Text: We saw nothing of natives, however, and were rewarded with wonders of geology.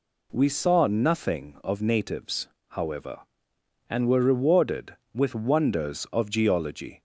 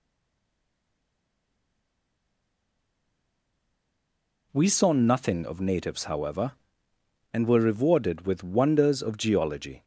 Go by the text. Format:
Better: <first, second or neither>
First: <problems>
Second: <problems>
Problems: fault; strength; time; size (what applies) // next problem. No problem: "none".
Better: first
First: none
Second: stays silent before the first word; strong; until 4.5 s; 4.5 s long